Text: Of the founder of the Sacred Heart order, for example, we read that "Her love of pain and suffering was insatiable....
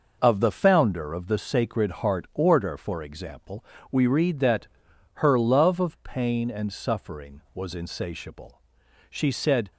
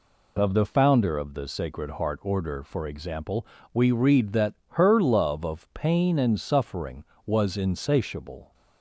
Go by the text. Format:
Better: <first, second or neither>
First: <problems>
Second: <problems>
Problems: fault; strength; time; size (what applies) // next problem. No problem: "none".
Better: second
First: pauses between "that" and "Her"; noticeable; at 4.6 s; 0.46 s long // goes on to say "She said"; noticeable; from 9.0 s on; 0.62 s long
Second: pauses between "that" and "Her"; slight; at 4.5 s; 0.16 s long